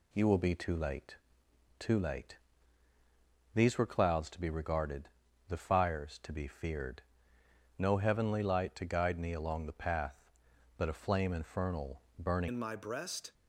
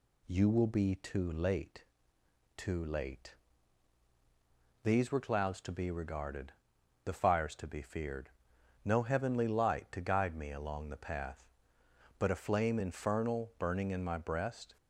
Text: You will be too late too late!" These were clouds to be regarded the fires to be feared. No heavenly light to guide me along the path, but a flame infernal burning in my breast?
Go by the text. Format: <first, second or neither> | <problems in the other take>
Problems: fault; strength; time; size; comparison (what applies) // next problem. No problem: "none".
second | pauses between "late" and "too"; noticeable; at 1.1 s; 0.64 s long; noticeable in the second // pauses between "regarded" and "the"; at 5.0 s; 0.40 s long; noticeable in the second // pauses between "infernal" and "burning"; slight; at 12.0 s; 0.18 s long // changes voice at "in"; from 12.4 s on; 0.9 s long